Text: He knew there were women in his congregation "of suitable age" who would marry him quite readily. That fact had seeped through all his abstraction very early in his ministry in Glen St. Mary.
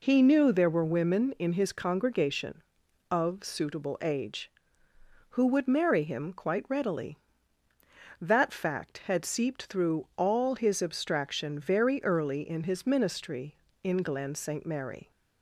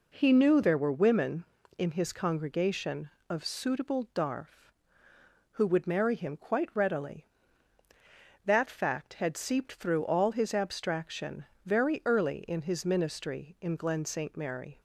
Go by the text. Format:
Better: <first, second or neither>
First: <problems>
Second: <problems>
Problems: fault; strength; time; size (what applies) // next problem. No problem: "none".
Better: first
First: none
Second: says "darf" for "age"; at 4.1 s // pauses between "abstraction" and "very"; slight; at 11.4 s; 0.18 s long